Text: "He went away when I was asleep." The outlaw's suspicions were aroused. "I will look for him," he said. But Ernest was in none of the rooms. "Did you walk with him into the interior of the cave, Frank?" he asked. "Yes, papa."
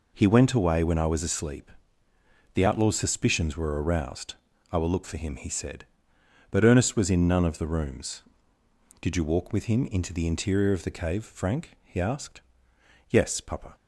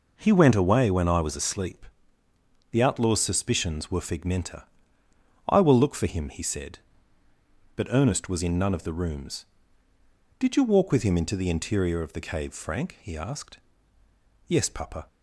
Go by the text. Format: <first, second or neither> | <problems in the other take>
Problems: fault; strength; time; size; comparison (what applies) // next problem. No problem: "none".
first | says "figmenta" for "aroused"; at 4.0 s